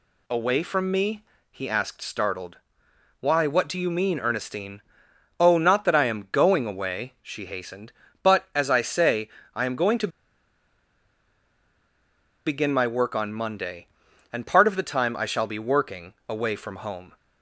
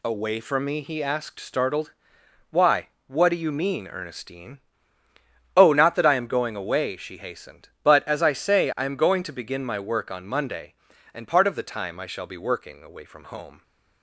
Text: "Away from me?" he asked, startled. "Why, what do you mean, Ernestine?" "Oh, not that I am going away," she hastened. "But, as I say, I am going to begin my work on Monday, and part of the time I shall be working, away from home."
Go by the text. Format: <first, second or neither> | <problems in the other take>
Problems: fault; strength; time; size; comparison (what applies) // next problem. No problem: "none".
second | pauses between "to" and "begin"; strong; at 10.0 s; 2.3 s long